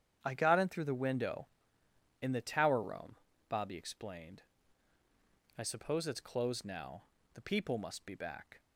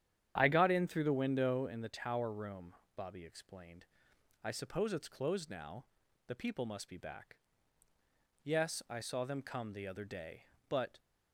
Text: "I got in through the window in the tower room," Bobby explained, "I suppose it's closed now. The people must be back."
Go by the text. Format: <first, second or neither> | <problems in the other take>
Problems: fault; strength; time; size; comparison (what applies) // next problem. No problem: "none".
first | starts louder than the rest; strong; until 1.3 s; 9.5 dB; strong in the first // goes on to say "Yes I saw them come the other day but"; strong; from 8.4 s on; 2.5 s long